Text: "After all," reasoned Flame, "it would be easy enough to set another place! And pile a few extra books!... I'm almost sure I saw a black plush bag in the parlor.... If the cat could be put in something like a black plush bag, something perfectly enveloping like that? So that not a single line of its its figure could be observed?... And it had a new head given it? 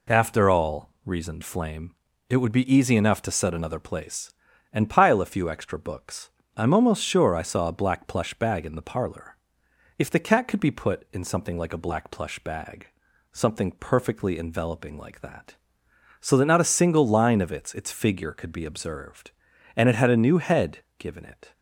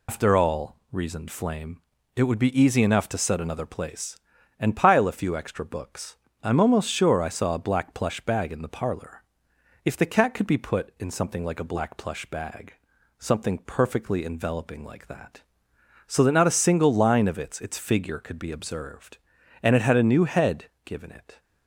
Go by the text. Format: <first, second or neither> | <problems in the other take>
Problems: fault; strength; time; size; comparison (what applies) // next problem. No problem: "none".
first | loses the start of "After"; at 0.0 s; 145 ms // pauses between "head" and "given"; slight; at 20.6 s; 0.20 s long; slight in the first